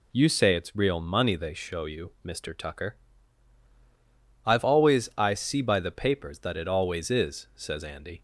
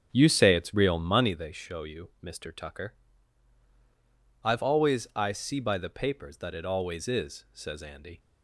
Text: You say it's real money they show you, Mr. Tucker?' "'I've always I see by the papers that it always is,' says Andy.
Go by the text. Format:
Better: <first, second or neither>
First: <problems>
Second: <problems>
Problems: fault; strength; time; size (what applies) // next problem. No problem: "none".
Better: first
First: none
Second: starts louder than the rest; strong; until 1.3 s; 8 dB